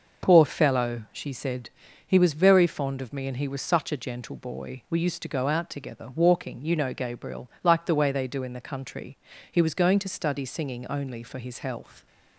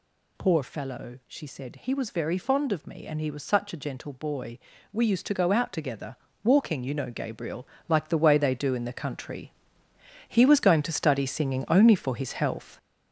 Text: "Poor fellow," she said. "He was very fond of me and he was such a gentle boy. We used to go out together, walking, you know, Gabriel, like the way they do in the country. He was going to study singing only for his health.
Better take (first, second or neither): first